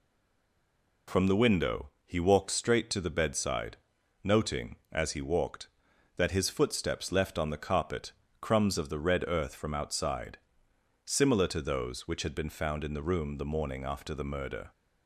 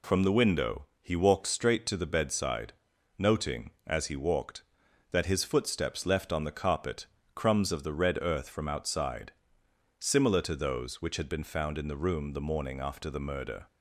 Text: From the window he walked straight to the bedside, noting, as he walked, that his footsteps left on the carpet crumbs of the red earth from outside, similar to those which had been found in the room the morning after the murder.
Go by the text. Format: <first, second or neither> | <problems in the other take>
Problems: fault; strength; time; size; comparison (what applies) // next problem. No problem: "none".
second | stays silent before the first word; until 1.0 s; 1.0 s long // pauses between "window" and "he"; slight; at 1.8 s; 0.16 s long; slight in the second // pauses between "carpet" and "crumbs"; slight; at 8.1 s; 0.28 s long; slight in the second